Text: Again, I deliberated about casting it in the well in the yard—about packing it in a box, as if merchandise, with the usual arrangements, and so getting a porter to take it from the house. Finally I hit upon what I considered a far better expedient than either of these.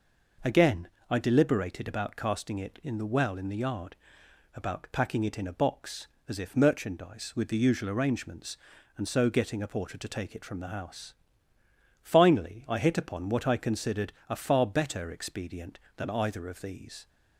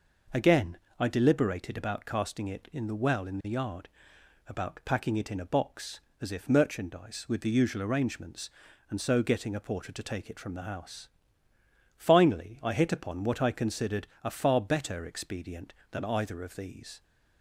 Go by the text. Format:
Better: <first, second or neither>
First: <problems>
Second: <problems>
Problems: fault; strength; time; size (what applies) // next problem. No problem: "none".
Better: neither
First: pauses between "considered" and "a"; slight; at 14.1 s; 0.18 s long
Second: pauses between "considered" and "a"; slight; at 14.0 s; 0.18 s long